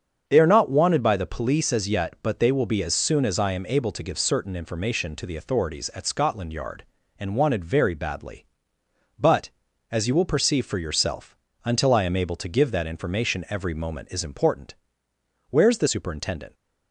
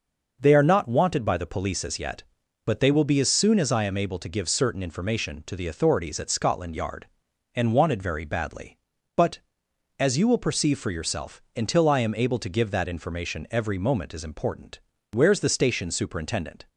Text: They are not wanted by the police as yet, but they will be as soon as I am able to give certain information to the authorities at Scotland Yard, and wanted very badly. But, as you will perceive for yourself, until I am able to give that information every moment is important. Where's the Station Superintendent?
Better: second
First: starts louder than the rest; strong; until 1.2 s; 7 dB // skips "Station"; at 15.8 s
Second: none

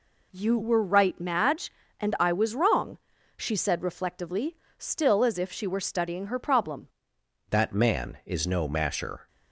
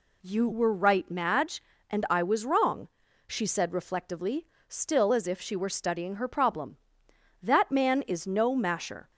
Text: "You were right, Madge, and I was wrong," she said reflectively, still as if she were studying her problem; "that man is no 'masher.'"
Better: second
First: changes voice at "that"; from 7.5 s on; 1.7 s long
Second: none

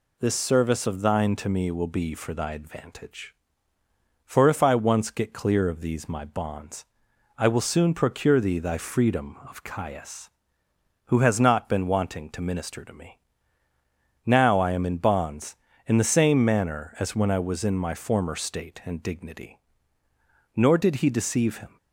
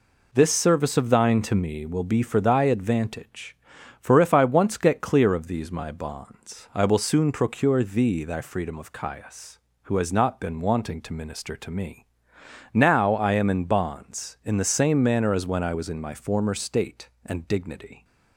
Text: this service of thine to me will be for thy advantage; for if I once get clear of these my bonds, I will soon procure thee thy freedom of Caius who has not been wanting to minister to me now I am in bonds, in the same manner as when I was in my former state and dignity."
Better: second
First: pauses between "me" and "now"; at 13.1 s; 1.0 s long // goes on to say "Nor did he deceive him"; noticeable; from 20.5 s on; 1.1 s long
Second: pauses between "me" and "now"; noticeable; at 12.0 s; 0.70 s long

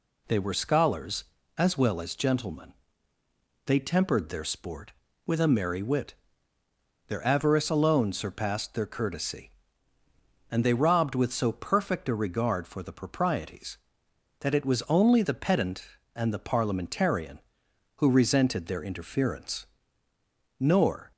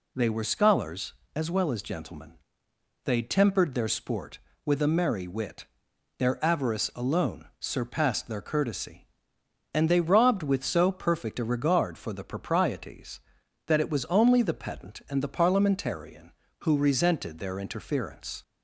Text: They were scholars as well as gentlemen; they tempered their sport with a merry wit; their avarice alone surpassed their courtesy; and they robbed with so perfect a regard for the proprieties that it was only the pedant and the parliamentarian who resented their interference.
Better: second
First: goes on to say "Nor"; from 20.5 s on; 0.52 s long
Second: none

